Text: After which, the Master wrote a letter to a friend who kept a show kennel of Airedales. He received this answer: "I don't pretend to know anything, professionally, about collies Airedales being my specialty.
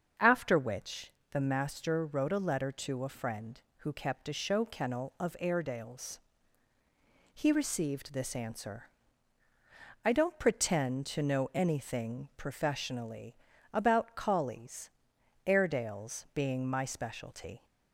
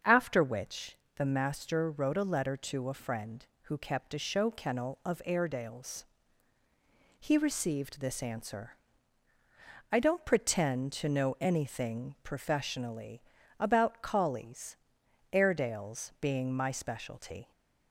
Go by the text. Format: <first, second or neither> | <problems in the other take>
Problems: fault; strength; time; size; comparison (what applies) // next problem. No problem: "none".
neither | starts louder than the rest; the same in both // pauses between "collies" and "Airedales"; noticeable; the same in both